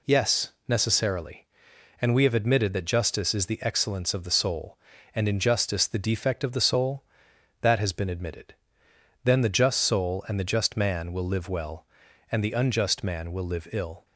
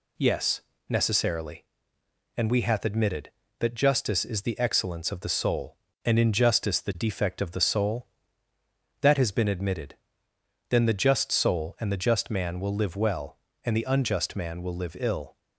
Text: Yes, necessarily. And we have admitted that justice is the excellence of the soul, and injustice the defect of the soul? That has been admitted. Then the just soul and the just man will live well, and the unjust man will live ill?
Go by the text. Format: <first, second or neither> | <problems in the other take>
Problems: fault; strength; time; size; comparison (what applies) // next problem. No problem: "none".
first | says "hath" for "have"; at 2.6 s